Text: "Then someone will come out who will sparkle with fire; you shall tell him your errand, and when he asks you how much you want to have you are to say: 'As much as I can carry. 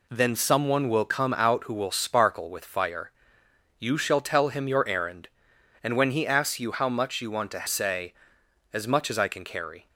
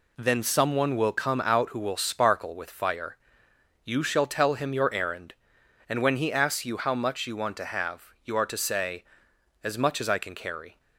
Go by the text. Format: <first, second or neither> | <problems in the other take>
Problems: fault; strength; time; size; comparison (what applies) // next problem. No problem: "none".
second | skips "have you are to"; at 7.6 s